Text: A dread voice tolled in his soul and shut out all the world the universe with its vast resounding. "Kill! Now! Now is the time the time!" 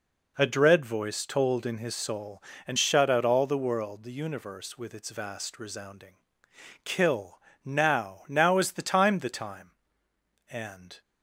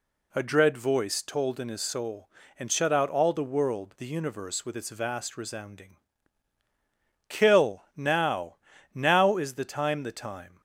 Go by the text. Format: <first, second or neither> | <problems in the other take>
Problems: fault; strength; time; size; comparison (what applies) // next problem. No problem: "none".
second | goes on to say "And"; from 10.4 s on; 0.52 s long